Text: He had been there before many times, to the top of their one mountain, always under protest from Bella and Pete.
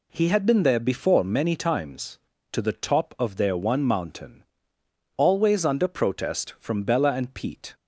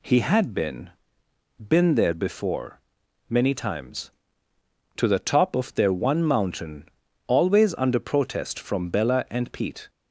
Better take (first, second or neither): first